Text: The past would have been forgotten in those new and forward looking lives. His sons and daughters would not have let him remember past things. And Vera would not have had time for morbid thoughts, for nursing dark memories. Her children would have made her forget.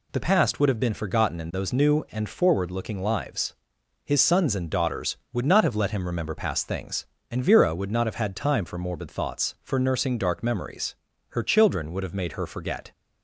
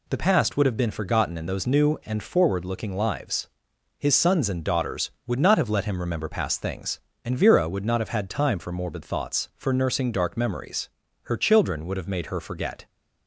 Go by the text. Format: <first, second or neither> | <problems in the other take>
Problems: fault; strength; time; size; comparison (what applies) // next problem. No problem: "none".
neither | none